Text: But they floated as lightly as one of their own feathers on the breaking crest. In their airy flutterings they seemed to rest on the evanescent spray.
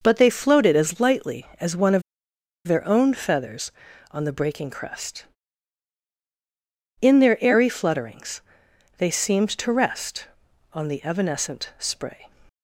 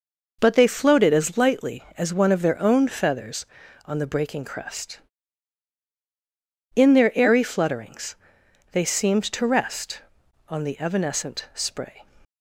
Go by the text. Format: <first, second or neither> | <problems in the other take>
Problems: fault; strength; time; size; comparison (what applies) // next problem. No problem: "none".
second | pauses between "of" and "their"; noticeable; at 2.0 s; 0.65 s long // pauses between "flutterings" and "they"; noticeable; at 8.4 s; 0.56 s long; noticeable in the second